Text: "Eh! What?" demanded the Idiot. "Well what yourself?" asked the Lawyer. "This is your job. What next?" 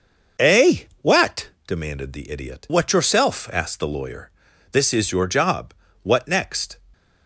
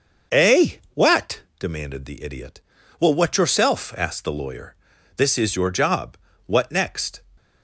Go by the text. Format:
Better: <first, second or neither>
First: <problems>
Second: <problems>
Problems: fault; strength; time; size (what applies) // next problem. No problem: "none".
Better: second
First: starts louder than the rest; noticeable; until 1.7 s; 6 dB // skips "Well"; at 2.6 s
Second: starts louder than the rest; until 1.6 s; 6.5 dB